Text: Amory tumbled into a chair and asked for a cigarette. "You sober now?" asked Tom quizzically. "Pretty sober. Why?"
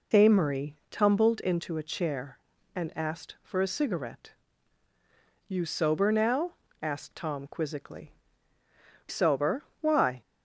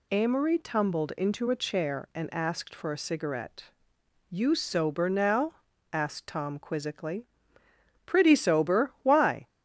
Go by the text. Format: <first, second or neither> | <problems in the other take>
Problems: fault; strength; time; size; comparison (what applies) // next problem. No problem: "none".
second | skips "Pretty"; at 8.6 s